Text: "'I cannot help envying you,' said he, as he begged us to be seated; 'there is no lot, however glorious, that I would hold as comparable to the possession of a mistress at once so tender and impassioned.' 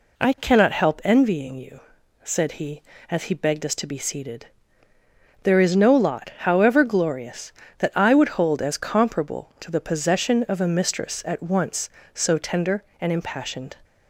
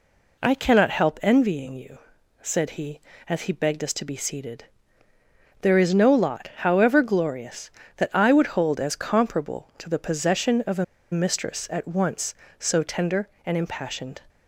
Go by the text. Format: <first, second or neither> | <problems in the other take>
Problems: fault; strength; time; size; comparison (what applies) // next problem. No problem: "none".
first | pauses between "a" and "mistress"; slight; at 10.8 s; 0.27 s long